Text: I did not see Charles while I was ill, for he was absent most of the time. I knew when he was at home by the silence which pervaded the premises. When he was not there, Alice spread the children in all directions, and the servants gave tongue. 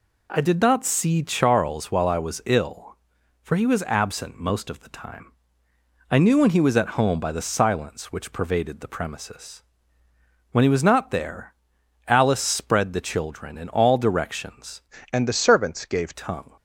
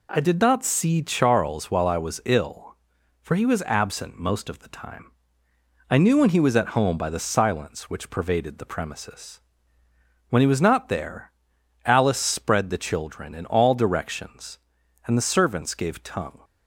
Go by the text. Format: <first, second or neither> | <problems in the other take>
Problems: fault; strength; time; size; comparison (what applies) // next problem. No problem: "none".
second | changes voice from "and" to "gave"; from 15.1 to 16.1 s; 1.0 s long